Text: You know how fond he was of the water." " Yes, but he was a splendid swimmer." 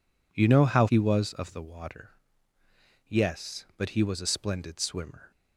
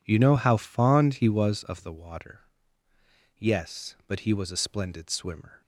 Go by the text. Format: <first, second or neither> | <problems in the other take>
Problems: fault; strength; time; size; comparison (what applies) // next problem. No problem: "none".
second | skips "fond"; at 0.8 s